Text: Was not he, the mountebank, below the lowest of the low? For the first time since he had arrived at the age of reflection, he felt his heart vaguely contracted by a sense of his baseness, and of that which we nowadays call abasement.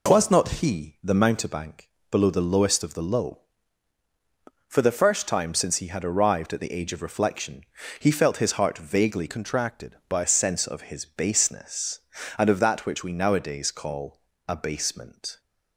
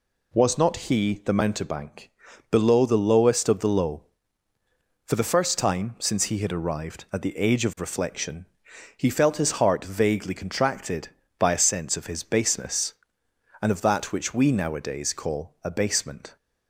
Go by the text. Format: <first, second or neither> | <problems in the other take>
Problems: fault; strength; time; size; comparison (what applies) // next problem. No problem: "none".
second | changes voice from "contracted" to "by"; from 9.2 to 10.2 s; 1.0 s long // pauses between "call" and "abasement"; slight; at 14.2 s; 0.26 s long